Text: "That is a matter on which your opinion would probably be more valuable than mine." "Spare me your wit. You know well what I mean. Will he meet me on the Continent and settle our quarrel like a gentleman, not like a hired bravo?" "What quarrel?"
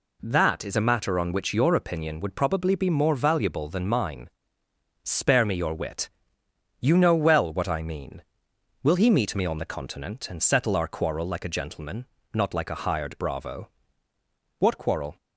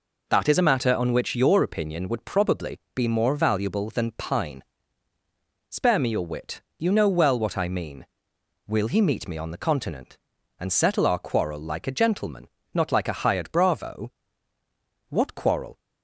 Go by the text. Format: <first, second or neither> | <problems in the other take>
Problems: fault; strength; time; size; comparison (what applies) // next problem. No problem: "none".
first | pauses between "probably" and "be"; slight; at 2.7 s; 0.16 s long // says "pine" for "mine"; at 4.1 s